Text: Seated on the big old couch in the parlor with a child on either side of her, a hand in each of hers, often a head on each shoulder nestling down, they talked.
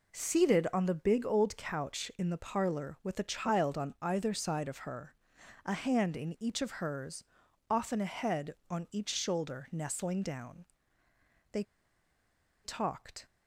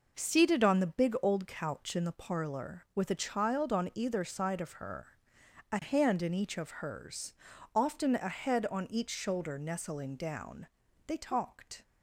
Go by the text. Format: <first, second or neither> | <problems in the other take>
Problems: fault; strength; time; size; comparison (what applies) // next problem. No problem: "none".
second | pauses between "they" and "talked"; at 11.6 s; 1.0 s long